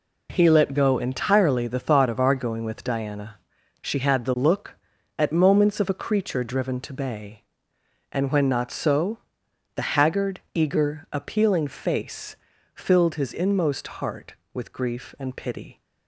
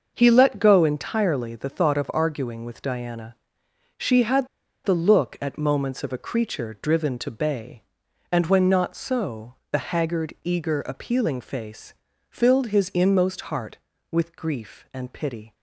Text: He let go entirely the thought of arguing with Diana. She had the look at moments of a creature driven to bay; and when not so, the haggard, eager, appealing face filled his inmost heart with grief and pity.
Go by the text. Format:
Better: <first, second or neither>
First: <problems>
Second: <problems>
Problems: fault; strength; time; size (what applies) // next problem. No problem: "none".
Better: first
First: pauses between "face" and "filled"; at 12.3 s; 0.40 s long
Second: starts louder than the rest; until 1.1 s; 6 dB // pauses between "had" and "the"; at 4.4 s; 0.36 s long // pauses between "face" and "filled"; at 11.9 s; 0.38 s long